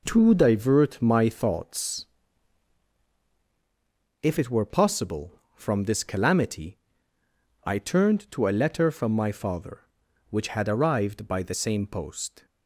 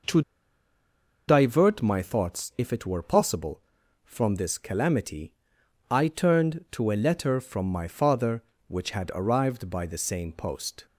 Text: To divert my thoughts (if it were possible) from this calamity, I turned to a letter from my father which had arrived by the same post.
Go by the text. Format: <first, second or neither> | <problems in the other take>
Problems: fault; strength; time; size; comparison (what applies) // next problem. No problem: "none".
first | pauses between "To" and "divert"; at 0.2 s; 1.0 s long